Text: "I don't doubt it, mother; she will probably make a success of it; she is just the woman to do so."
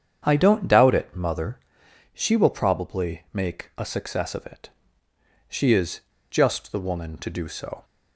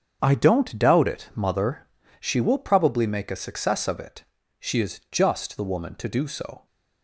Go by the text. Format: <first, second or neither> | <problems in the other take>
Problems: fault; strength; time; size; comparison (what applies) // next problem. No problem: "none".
second | starts louder than the rest; strong; until 1.2 s; 8 dB; strong in the second // pauses between "is" and "just"; slight; at 5.9 s; 0.30 s long